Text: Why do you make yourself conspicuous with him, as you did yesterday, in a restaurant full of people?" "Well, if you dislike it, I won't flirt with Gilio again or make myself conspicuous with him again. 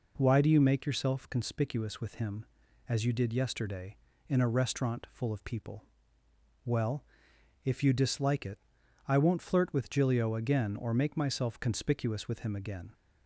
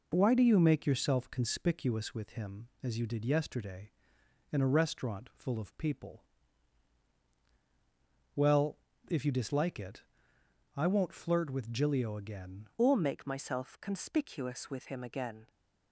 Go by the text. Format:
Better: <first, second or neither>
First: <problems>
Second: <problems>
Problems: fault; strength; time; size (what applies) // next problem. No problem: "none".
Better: first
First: none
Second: changes voice at "or"; from 12.7 s on; 2.7 s long